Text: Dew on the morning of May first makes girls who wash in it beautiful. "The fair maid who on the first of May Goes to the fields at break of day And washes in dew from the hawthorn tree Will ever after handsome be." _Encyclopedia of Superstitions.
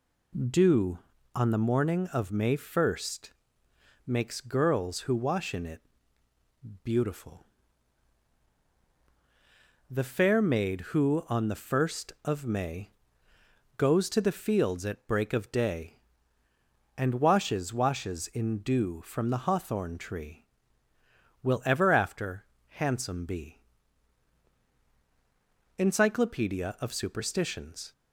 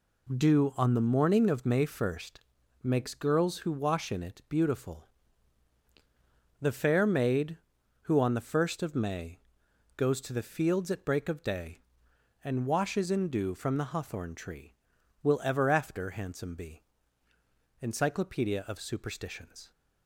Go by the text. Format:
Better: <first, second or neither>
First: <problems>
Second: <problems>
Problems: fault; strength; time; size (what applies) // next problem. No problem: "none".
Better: second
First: pauses between "first" and "makes"; noticeable; at 3.3 s; 0.74 s long // pauses between "it" and "beautiful"; at 5.8 s; 1.0 s long // pauses between "May" and "Goes"; noticeable; at 12.8 s; 0.90 s long // says "washes" twice; at 17.7 s // pauses between "after" and "handsome"; slight; at 22.4 s; 0.22 s long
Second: pauses between "first" and "makes"; at 2.4 s; 0.42 s long // pauses between "May" and "Goes"; noticeable; at 9.3 s; 0.56 s long